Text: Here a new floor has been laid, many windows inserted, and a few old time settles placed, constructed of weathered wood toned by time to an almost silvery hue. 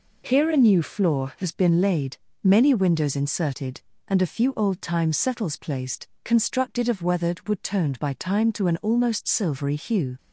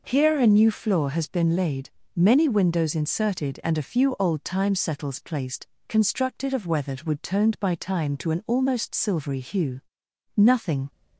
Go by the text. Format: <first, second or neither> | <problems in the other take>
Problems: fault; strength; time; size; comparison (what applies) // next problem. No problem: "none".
first | goes on to say "Nothing"; from 10.3 s on; 0.54 s long